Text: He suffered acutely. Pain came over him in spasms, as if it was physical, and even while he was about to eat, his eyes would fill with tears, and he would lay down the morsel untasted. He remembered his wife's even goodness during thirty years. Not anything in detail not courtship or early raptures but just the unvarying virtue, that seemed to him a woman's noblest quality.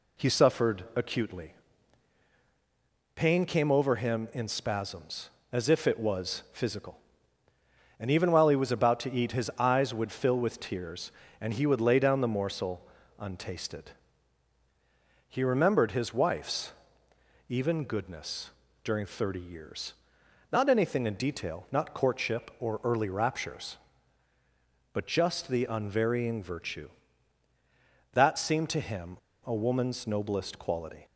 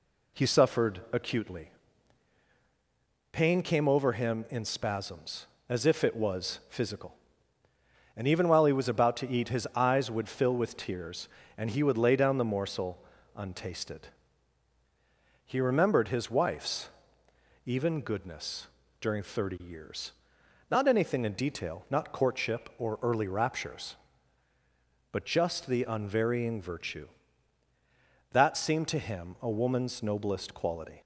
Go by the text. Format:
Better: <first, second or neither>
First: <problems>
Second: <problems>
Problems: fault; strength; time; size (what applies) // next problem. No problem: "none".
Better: second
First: pauses between "morsel" and "untasted"; slight; at 12.8 s; 0.32 s long // pauses between "wife's" and "even"; noticeable; at 16.7 s; 0.76 s long // pauses between "goodness" and "during"; slight; at 18.4 s; 0.32 s long // pauses between "him" and "a"; slight; at 29.1 s; 0.28 s long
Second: pauses between "morsel" and "untasted"; slight; at 13.0 s; 0.32 s long // pauses between "wife's" and "even"; noticeable; at 16.8 s; 0.76 s long // pauses between "goodness" and "during"; slight; at 18.6 s; 0.32 s long